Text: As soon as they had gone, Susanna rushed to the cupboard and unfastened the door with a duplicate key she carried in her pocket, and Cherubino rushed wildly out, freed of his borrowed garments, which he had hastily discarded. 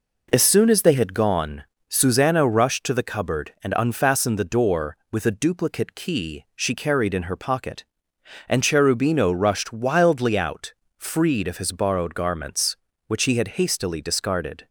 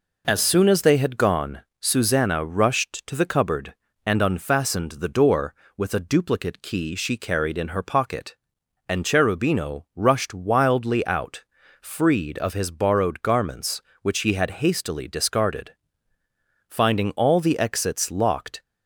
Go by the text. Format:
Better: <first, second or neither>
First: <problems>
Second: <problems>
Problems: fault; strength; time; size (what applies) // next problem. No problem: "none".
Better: first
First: none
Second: goes on to say "Finding all the exits locked"; strong; from 16.6 s on; 1.9 s long